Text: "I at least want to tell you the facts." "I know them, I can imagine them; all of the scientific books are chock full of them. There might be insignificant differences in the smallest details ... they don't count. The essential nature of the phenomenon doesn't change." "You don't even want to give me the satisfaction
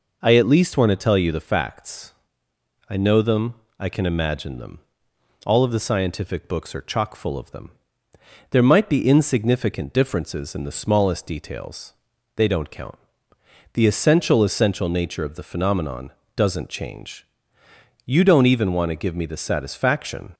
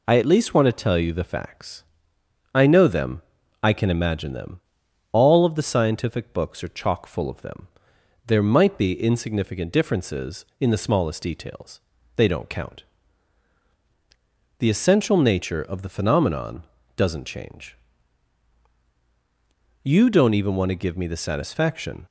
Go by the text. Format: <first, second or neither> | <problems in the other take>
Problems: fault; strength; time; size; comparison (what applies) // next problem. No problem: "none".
second | says "essential" twice; at 14.4 s // pauses between "phenomenon" and "doesn't"; slight; at 16.1 s; 0.24 s long; slight in the second